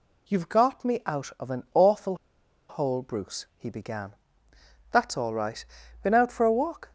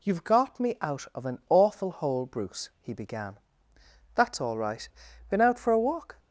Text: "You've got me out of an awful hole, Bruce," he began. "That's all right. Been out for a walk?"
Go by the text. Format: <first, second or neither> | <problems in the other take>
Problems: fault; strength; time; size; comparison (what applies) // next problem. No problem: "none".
second | pauses between "awful" and "hole"; noticeable; at 2.1 s; 0.53 s long